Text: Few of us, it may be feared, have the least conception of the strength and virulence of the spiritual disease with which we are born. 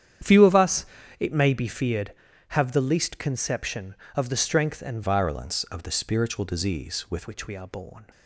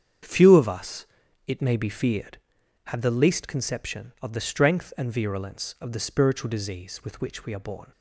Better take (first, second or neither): second